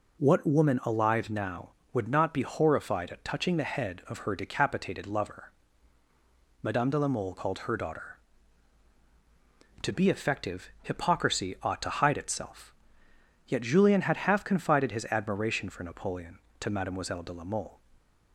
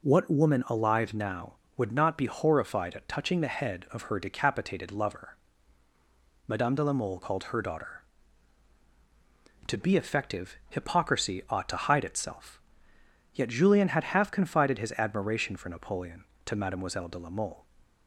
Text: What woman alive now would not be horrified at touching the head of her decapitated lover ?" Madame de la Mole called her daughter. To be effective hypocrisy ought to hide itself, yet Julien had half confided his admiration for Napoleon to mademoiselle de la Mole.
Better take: neither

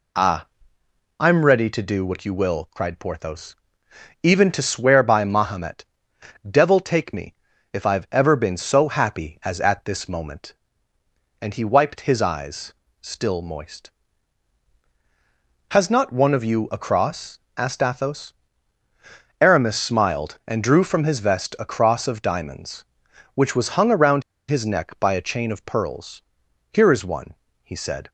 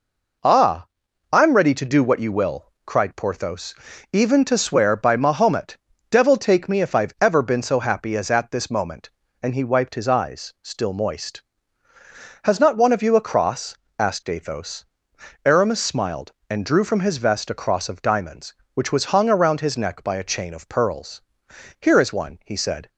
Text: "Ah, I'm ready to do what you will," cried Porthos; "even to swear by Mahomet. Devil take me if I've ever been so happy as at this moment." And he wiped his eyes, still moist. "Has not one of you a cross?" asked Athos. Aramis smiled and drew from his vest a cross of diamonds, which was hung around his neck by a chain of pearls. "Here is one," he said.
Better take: second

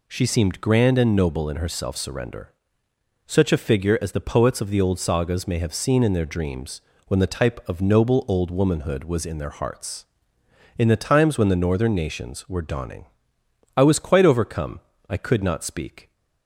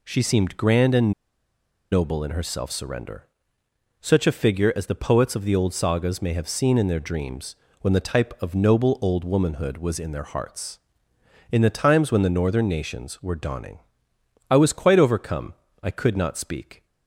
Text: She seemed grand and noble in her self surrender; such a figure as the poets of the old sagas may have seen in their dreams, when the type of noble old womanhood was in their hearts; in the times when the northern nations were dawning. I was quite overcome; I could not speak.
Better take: first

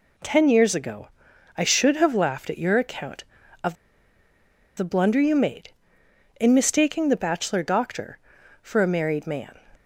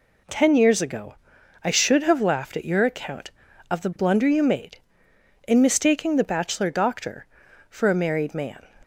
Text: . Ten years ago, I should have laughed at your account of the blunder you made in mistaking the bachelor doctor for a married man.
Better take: second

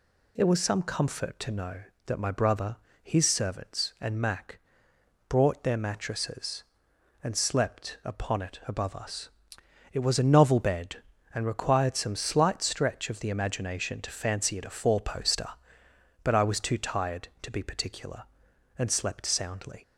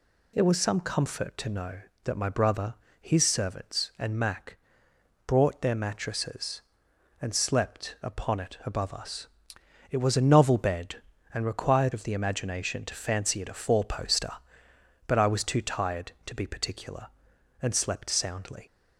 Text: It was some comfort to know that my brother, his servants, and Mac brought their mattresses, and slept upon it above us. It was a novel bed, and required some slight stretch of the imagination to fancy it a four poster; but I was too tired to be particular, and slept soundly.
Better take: first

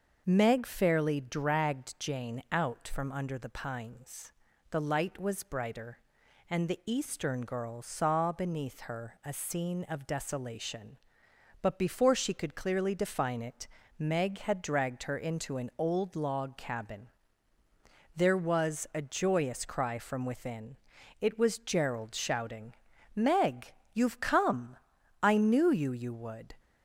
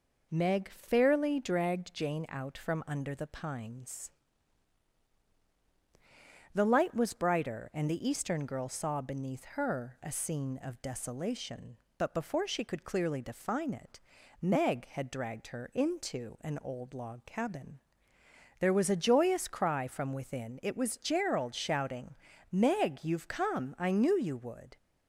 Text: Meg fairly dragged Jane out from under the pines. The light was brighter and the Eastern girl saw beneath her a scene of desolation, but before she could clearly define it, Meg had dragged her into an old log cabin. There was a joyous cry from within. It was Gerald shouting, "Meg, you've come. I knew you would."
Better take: second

